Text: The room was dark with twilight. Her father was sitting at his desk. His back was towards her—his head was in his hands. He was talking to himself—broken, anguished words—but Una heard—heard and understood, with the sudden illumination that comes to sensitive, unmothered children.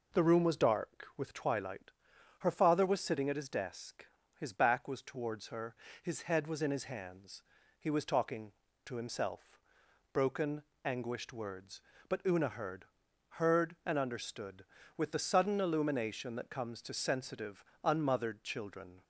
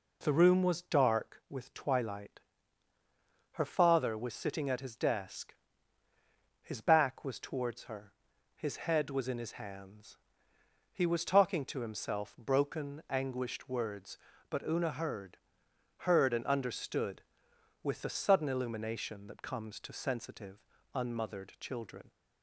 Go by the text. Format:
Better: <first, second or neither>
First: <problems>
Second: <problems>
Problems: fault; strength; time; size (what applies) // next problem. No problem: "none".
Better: neither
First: none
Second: none